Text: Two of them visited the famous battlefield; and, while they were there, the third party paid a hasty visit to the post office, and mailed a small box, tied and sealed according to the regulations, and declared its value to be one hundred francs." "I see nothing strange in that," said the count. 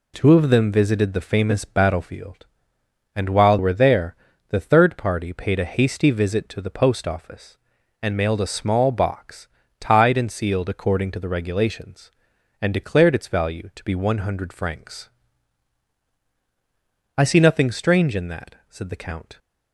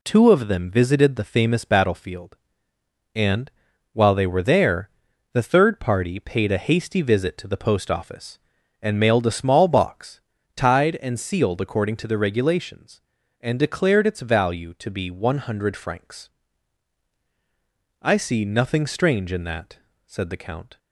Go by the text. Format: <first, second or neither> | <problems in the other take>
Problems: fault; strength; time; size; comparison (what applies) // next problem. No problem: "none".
second | skips "they"; at 3.5 s